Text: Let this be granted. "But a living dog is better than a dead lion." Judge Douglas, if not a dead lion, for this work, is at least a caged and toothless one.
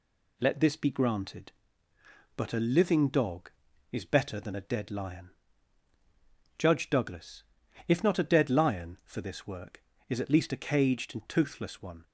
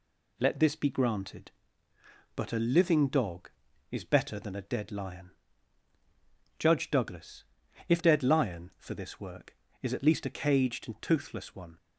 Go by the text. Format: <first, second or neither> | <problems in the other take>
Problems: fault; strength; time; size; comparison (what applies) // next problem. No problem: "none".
first | skips "not a"; at 8.0 s